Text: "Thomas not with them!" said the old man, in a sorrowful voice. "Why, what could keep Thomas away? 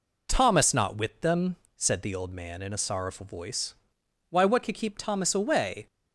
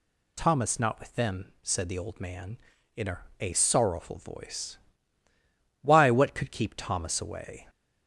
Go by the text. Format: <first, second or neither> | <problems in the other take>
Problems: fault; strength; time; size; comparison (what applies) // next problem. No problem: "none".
first | says "a" twice; at 3.4 s